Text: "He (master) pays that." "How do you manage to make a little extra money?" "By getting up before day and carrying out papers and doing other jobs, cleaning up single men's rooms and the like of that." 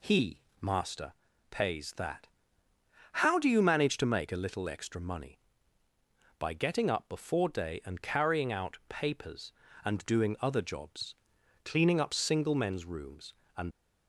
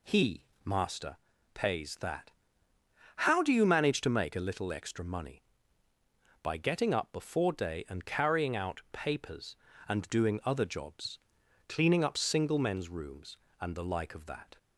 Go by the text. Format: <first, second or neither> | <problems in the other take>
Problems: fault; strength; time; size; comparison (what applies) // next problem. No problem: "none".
second | stops before "the like of that"; at 13.7 s